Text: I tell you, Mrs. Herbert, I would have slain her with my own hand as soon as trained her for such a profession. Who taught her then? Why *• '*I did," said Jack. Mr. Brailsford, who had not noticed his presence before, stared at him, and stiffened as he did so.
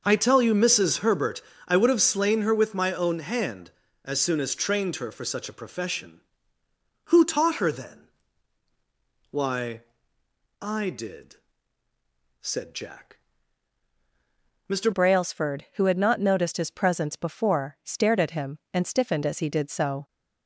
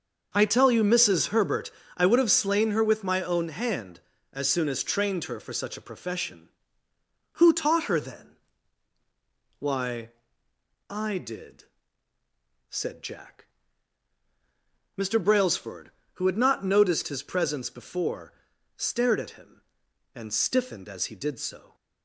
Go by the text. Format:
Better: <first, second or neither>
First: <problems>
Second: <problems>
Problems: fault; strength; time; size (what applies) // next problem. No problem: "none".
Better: second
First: starts louder than the rest; noticeable; until 1.0 s; 6 dB // changes voice at "Brailsford"; from 14.9 s on; 5.1 s long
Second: starts louder than the rest; noticeable; until 1.3 s; 6 dB